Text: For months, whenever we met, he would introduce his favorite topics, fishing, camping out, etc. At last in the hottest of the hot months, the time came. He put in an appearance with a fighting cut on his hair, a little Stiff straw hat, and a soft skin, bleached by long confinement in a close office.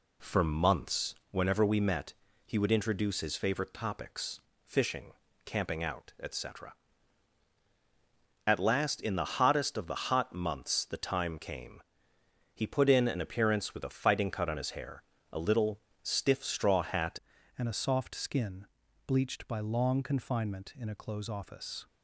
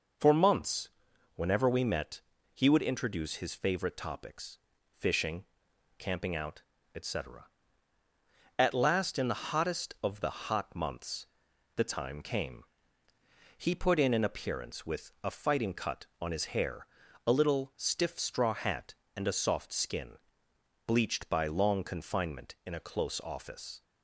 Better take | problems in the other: second | pauses between "little" and "Stiff"; slight; at 15.8 s; 0.22 s long // changes voice at "and"; from 17.5 s on; 4.3 s long

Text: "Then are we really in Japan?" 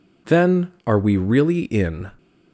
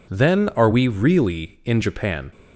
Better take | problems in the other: second | stops before "Japan"; at 2.1 s

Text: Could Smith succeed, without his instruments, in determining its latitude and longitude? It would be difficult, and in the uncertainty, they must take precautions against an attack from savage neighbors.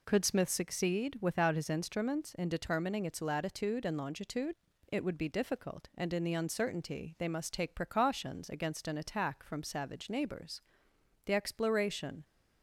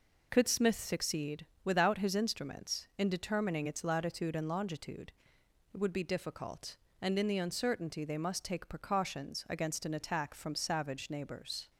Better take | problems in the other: second | goes on to say "The exploration"; noticeable; from 11.2 s on; 0.98 s long

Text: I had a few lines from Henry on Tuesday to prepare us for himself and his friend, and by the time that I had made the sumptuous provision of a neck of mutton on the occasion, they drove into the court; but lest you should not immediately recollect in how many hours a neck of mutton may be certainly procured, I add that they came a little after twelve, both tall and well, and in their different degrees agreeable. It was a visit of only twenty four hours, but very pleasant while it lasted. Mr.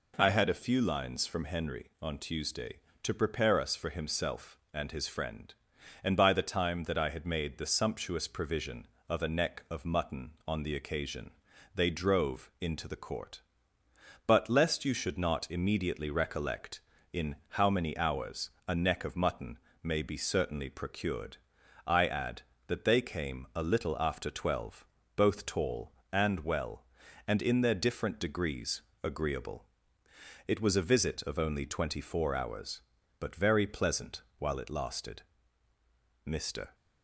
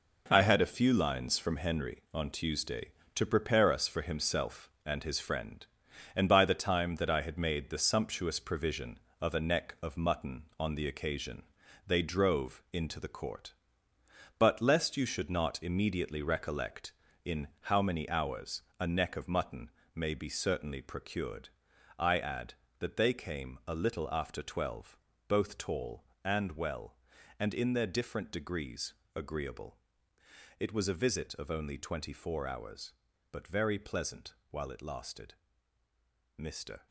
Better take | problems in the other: first | gets quieter; strong; throughout; 8.5 dB // pauses between "hours" and "a"; slight; at 18.6 s; 0.18 s long; slight in the first // pauses between "mutton" and "may"; slight; at 19.7 s; 0.24 s long; slight in the first // pauses between "degrees" and "agreeable"; slight; at 28.9 s; 0.22 s long; slight in the first // pauses between "pleasant" and "while"; slight; at 34.3 s; 0.18 s long; slight in the first

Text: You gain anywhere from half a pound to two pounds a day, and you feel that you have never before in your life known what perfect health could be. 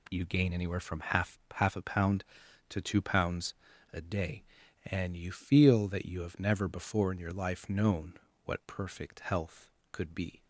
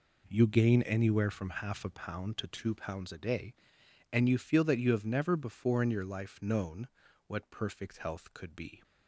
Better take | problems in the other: second | says "half" twice; at 1.5 s // pauses between "pounds" and "a"; at 3.5 s; 0.38 s long // pauses between "known" and "what"; slight; at 8.1 s; 0.32 s long; also in the second

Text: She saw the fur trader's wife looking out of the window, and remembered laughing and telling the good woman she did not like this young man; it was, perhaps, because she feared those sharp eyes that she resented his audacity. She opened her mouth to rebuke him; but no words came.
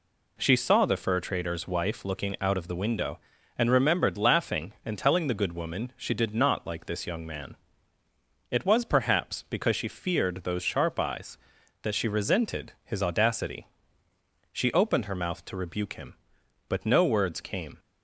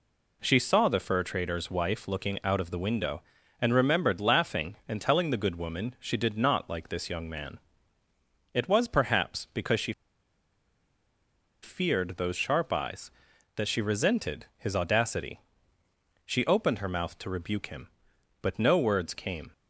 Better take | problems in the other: first | pauses between "she" and "feared"; strong; at 9.9 s; 1.6 s long

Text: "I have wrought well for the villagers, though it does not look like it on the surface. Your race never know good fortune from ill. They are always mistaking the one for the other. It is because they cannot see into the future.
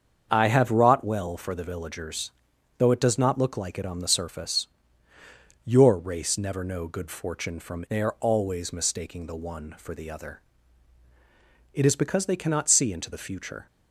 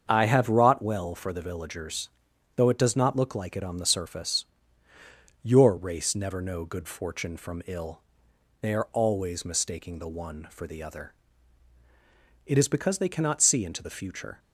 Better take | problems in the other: second | starts louder than the rest; until 1.3 s; 7 dB; strong in the second // skips "ill"; at 7.8 s

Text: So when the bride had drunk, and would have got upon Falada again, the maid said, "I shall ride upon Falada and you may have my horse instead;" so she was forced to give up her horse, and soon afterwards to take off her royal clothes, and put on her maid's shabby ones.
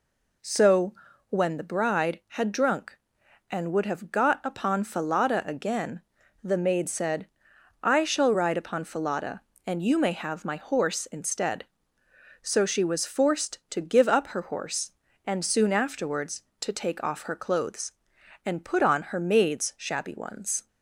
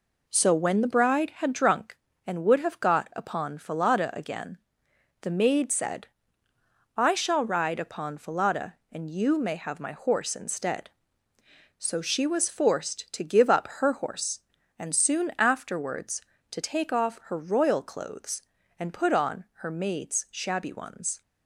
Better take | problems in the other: second | pauses between "So" and "when"; slight; at 0.9 s; 0.34 s long // skips "royal"; at 17.3 s

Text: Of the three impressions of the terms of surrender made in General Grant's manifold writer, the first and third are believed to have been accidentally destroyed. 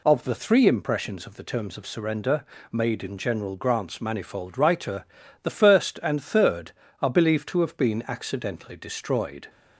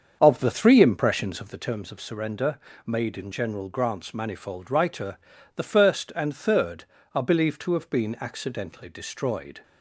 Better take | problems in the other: first | starts louder than the rest; until 1.8 s; 7 dB // pauses between "surrender" and "made"; slight; at 2.5 s; 0.26 s long; slight in the first

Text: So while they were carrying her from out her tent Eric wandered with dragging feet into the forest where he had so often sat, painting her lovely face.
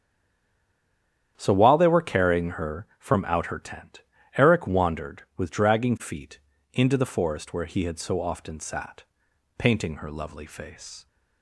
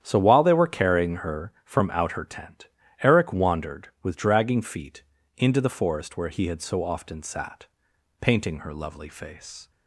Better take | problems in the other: second | stays silent before the first word; noticeable; until 1.3 s; 1.3 s long // starts louder than the rest; strong; until 2.3 s; 9.5 dB; strong in the second // pauses between "tent" and "Eric"; slight; at 4.0 s; 0.36 s long; slight in the second // pauses between "feet" and "into"; slight; at 6.3 s; 0.34 s long; slight in the second

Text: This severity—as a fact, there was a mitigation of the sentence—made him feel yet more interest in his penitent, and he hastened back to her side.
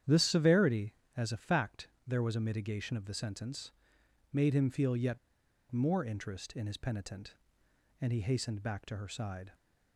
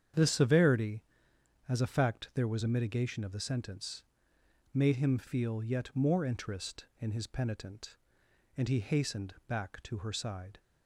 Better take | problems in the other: second | starts louder than the rest; strong; until 1.2 s; 9.5 dB; strong in the second // pauses between "yet" and "more"; noticeable; at 5.1 s; 0.53 s long

